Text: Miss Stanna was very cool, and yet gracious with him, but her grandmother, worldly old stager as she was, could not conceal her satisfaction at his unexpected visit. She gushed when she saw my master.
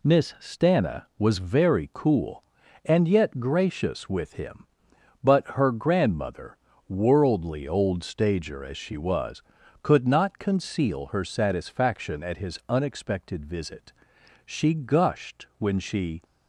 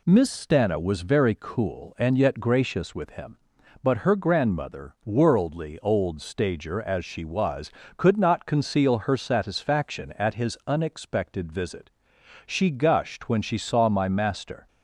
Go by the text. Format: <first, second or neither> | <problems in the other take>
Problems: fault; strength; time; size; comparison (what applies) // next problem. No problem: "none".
second | stops before "saw my master"; at 16.2 s